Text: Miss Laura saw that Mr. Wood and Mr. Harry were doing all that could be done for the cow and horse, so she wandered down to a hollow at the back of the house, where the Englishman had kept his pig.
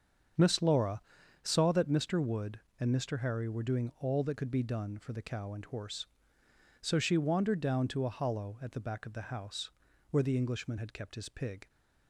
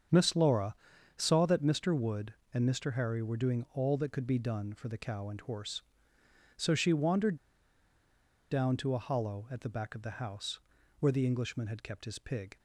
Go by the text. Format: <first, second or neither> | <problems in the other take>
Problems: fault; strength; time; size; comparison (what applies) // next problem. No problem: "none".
first | starts louder than the rest; strong; until 1.5 s; 7.5 dB; strong in the first // pauses between "Laura" and "saw"; at 0.7 s; 0.42 s long; also in the first // pauses between "wandered" and "down"; at 7.3 s; 1.1 s long